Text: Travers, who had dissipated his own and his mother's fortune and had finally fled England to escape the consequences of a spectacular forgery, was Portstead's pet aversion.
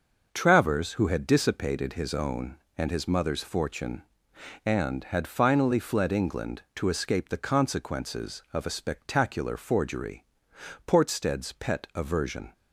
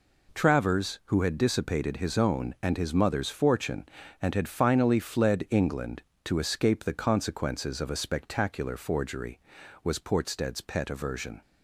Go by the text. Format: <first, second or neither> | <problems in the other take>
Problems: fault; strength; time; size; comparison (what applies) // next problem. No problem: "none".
second | skips "was"; at 10.5 s